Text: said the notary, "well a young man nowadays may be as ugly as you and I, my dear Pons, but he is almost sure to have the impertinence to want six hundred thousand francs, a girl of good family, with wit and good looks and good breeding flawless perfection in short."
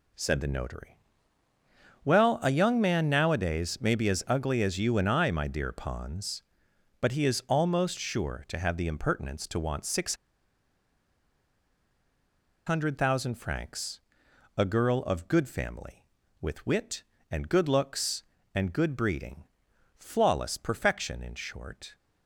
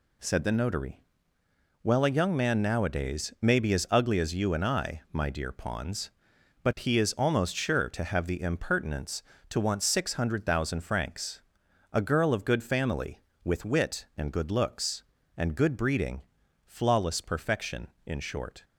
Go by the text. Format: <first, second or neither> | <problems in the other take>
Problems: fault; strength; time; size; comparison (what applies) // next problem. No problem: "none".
second | pauses between "six" and "hundred"; strong; at 10.1 s; 2.5 s long // pauses between "breeding" and "flawless"; noticeable; at 19.4 s; 0.56 s long; also in the second